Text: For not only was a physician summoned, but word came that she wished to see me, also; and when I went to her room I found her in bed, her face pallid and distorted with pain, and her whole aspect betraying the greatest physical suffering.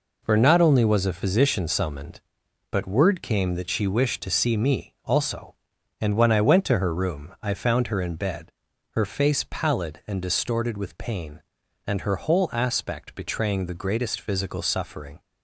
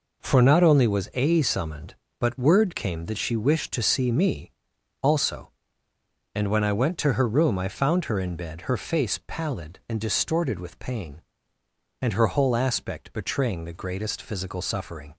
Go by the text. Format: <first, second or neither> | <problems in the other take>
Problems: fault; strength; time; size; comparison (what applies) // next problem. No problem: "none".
first | skips "physician"; at 1.4 s